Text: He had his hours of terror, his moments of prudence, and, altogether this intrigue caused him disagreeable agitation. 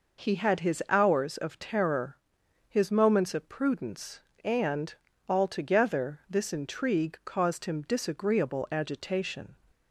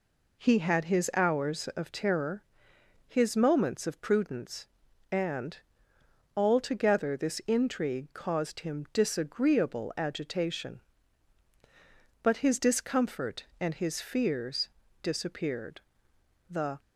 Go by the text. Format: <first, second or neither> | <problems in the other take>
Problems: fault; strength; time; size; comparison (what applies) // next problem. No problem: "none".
first | goes on to say "But his discomfort and his fears disappeared The"; strong; from 12.2 s on; 4.5 s long